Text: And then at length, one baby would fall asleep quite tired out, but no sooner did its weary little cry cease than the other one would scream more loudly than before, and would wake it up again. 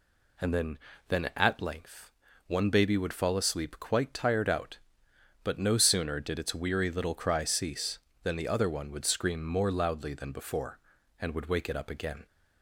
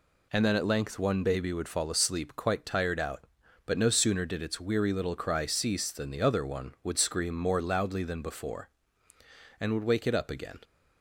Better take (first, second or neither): second